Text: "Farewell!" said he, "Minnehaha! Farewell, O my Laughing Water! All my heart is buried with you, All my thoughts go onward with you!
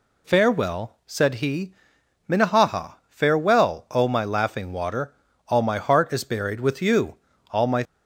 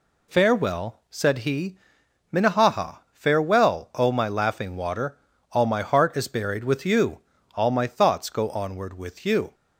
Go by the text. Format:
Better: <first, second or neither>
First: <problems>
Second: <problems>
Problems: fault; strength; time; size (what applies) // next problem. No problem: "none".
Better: second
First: stops before "thoughts go onward with you"; at 7.8 s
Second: none